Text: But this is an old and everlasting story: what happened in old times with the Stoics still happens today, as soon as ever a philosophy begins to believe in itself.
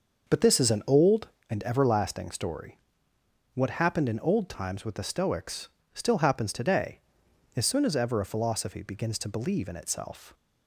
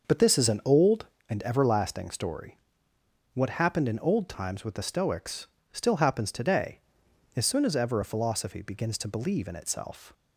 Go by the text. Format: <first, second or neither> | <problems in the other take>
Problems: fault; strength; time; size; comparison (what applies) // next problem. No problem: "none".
neither | starts louder than the rest; the same in both // pauses between "Stoics" and "still"; slight; the same in both